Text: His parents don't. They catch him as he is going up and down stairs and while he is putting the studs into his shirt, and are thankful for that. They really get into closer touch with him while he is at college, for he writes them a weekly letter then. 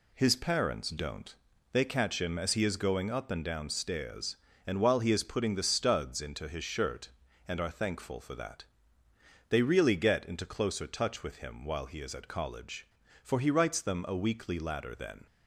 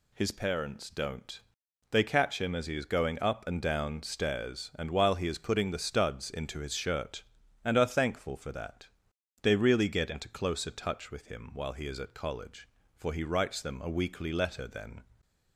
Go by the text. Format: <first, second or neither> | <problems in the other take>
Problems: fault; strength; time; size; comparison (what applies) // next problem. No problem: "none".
second | says "ladder" for "letter"; at 14.5 s